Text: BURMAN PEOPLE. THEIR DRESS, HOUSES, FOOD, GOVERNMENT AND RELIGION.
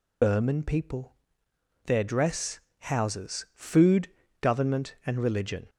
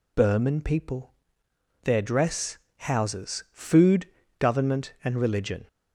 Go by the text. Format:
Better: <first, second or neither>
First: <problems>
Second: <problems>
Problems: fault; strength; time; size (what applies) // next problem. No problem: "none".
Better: second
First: loses the start of "BURMAN"; at 0.2 s; 45 ms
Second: none